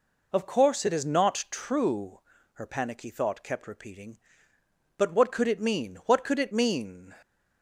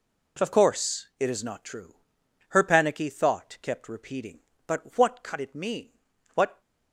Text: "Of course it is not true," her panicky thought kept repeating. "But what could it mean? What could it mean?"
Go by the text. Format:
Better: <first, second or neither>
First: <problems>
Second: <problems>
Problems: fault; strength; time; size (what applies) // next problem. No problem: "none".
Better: first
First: none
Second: stops before "could it mean"; at 6.6 s